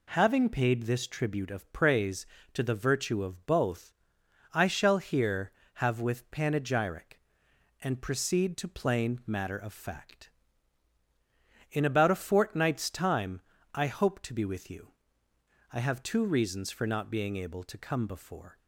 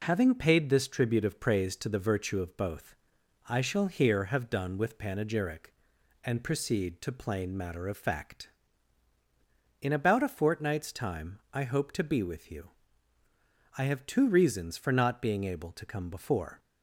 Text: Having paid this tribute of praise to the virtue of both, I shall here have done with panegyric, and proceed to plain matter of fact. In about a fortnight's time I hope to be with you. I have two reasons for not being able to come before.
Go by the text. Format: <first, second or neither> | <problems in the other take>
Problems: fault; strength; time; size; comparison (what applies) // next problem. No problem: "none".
second | skips "done"; at 6.0 s // pauses between "time" and "I"; slight; at 13.4 s; 0.32 s long